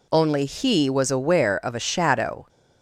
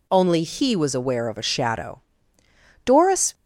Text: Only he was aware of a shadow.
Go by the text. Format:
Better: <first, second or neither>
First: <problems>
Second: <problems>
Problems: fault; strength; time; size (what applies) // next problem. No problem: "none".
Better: first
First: none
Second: goes on to say "Doris"; slight; from 2.8 s on; 0.48 s long